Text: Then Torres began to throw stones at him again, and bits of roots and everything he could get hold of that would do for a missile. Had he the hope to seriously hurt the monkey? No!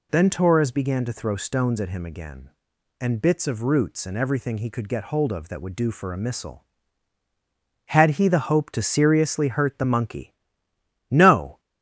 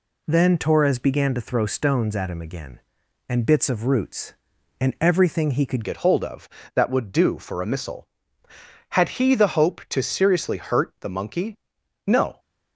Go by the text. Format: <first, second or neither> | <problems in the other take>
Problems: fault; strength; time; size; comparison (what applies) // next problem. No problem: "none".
first | changes voice at "get"; from 5.8 s on; 6.5 s long